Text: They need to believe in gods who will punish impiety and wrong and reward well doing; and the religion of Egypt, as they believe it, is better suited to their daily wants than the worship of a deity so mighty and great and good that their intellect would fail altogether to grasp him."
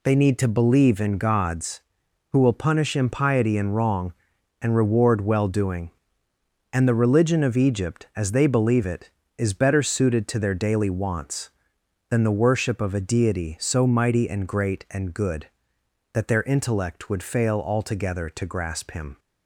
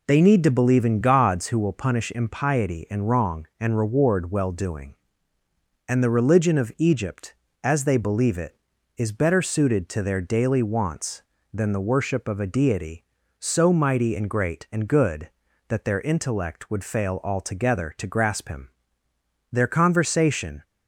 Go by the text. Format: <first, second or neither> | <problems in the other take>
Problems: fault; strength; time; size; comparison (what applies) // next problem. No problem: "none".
first | goes on to say "Their conversation"; noticeable; from 19.5 s on; 1.1 s long